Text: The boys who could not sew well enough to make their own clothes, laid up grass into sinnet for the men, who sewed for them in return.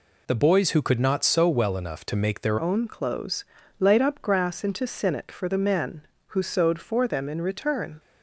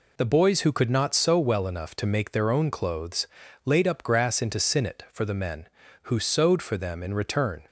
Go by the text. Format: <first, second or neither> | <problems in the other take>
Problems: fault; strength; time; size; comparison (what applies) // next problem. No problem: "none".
second | changes voice at "own"; from 2.5 s on; 5.4 s long